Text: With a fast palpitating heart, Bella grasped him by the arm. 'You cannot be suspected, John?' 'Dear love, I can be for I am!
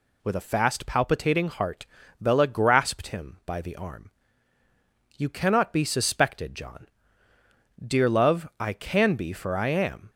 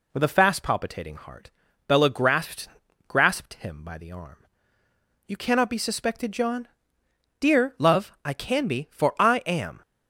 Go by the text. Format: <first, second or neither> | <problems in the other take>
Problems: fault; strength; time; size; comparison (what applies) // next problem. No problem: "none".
first | says "grasped" twice; at 3.0 s